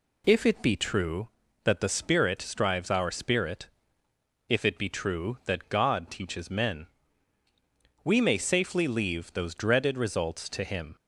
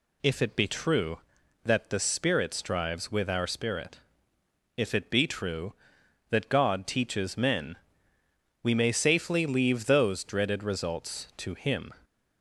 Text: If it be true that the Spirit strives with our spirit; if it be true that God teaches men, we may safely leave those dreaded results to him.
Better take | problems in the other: second | skips "with"; at 2.8 s

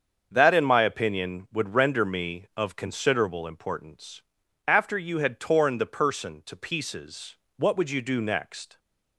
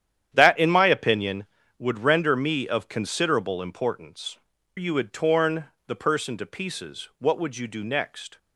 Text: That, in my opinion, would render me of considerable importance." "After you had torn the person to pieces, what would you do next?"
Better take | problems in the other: first | starts louder than the rest; strong; until 1.3 s; 10 dB; also in the first // skips "After"; at 4.5 s // pauses between "torn" and "the"; slight; at 5.6 s; 0.22 s long

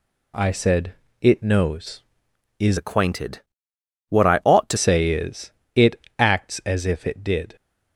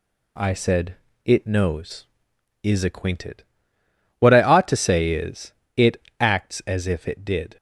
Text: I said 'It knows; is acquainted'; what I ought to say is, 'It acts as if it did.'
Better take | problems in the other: second | pauses between "said" and "It"; slight; at 0.9 s; 0.26 s long; slight in the second // changes voice from "acquainted" to "to"; from 2.7 to 4.7 s; 2.0 s long // pauses between "It" and "acts"; slight; at 5.9 s; 0.20 s long; slight in the second

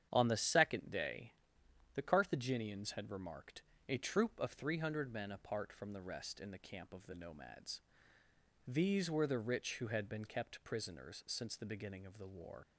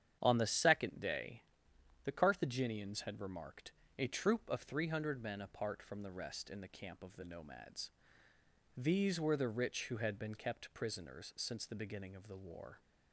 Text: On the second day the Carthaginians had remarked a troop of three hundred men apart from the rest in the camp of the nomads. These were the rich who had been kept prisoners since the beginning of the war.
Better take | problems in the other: second | starts louder than the rest; strong; until 1.1 s; 9 dB; strong in the second // pauses between "day" and "the"; noticeable; at 1.3 s; 0.62 s long; noticeable in the second // pauses between "remarked" and "a"; slight; at 3.6 s; 0.26 s long; slight in the second // leaves "war" unfinished; at 12.6 s; 75 ms

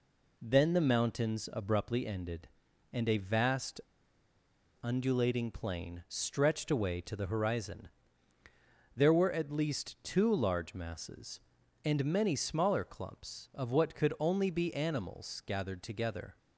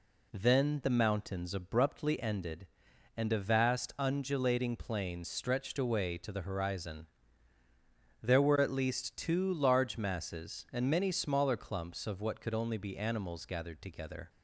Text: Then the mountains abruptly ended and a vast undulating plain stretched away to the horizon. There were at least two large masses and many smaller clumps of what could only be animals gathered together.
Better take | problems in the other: second | pauses between "vast" and "undulating"; at 3.8 s; 1.0 s long

